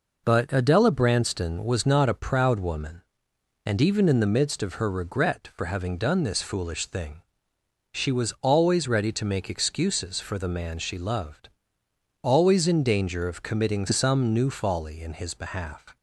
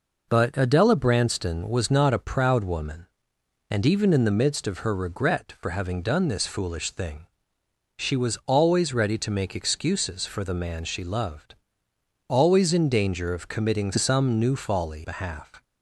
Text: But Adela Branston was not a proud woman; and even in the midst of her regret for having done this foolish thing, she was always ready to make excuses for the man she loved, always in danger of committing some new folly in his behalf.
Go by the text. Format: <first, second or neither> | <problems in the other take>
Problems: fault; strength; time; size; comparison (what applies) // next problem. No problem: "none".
first | skips "in his"; at 15.0 s